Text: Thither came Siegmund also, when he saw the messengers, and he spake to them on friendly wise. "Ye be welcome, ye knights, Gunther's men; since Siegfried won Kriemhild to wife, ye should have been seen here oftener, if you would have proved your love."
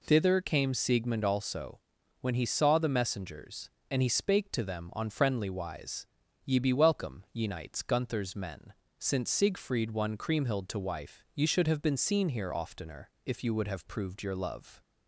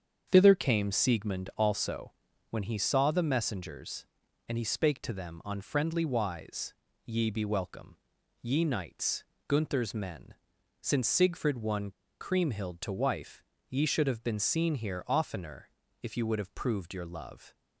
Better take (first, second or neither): first